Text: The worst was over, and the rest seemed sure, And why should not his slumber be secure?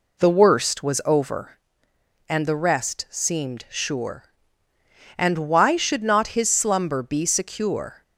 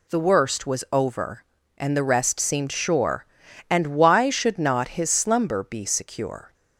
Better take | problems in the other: second | starts louder than the rest; slight; until 1.5 s; 2.5 dB

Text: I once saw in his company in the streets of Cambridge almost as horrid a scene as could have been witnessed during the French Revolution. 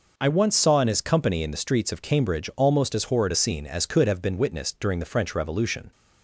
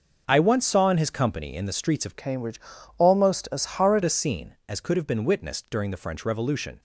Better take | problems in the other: first | starts louder than the rest; noticeable; until 1.2 s; 6 dB // changes voice from "Cambridge" to "horrid"; from 2.1 to 4.0 s; 1.9 s long // pauses between "Cambridge" and "almost"; at 2.6 s; 0.38 s long

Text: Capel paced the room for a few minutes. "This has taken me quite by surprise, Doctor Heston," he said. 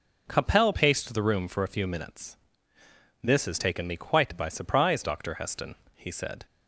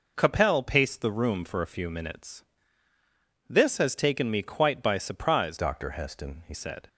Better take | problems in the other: first | changes voice from "Doctor" to "he"; from 5.5 to 6.5 s; 1.0 s long

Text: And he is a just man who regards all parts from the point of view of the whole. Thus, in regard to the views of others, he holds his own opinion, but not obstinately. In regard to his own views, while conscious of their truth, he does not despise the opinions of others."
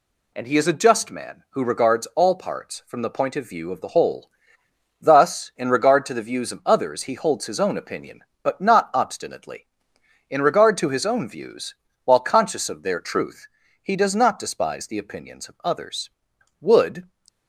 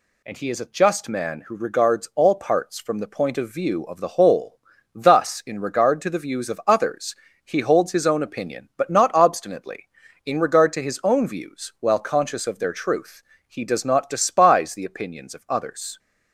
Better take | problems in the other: second | goes on to say "Wood"; slight; from 16.6 s on; 0.46 s long

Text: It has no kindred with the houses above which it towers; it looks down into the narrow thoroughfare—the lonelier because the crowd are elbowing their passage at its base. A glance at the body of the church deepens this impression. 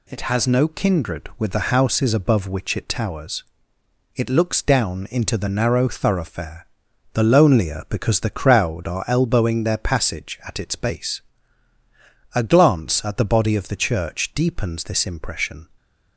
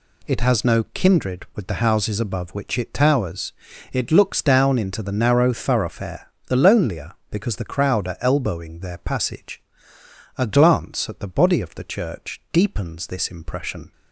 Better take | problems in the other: first | skips "at its base"; at 9.9 s

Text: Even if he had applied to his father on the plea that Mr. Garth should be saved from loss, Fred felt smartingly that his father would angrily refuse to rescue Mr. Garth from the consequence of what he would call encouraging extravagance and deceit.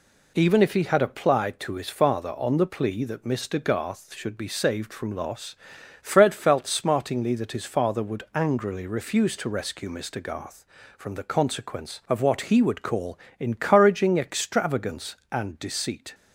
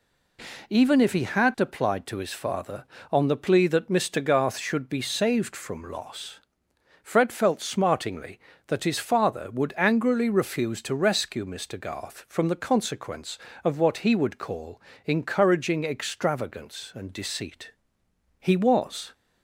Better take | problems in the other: first | pauses between "call" and "encouraging"; slight; at 14.8 s; 0.24 s long; slight in the first // goes on to say "He was"; noticeable; from 18.4 s on; 0.72 s long

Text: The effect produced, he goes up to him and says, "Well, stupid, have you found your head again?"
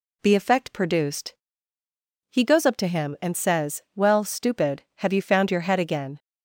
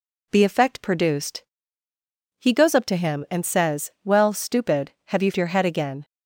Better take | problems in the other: first | skips "found"; at 5.3 s

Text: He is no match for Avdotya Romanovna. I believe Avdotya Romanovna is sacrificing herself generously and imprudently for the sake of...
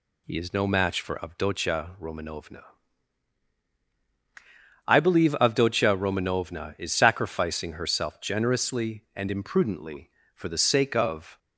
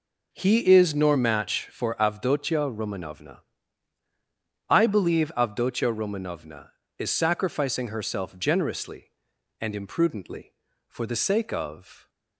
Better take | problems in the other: first | says "nor" for "no"; at 0.9 s

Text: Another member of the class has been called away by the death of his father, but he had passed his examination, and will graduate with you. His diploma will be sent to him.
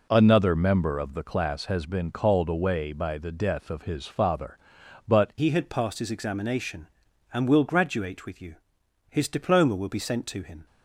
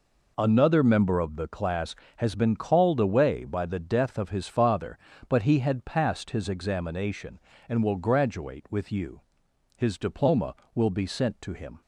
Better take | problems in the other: second | changes voice at "he"; from 5.3 s on; 5.3 s long

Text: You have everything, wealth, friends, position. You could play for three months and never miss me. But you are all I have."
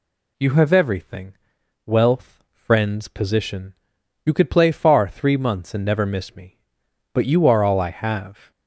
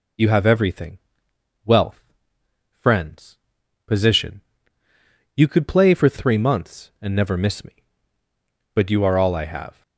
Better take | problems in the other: second | says "far" for "for"; at 4.7 s

